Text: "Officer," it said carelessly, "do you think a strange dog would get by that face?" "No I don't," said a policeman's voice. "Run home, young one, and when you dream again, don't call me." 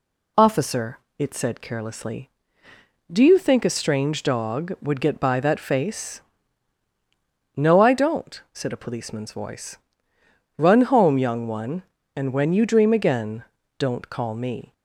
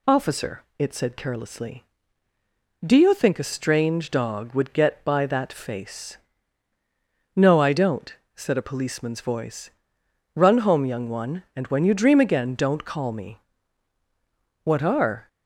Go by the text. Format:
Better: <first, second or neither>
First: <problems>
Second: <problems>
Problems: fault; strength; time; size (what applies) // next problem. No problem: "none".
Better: first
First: none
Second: goes on to say "What are"; noticeable; from 14.6 s on; 0.64 s long